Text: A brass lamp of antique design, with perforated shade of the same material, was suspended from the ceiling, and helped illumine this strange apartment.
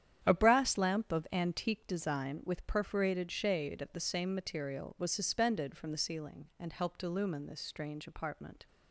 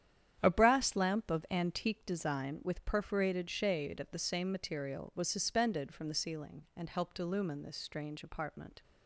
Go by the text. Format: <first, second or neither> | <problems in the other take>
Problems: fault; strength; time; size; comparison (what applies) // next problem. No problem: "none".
neither | starts louder than the rest; strong; the same in both